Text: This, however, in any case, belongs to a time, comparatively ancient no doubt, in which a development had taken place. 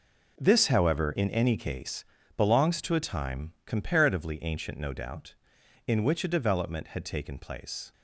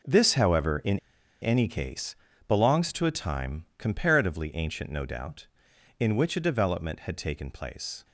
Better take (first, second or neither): first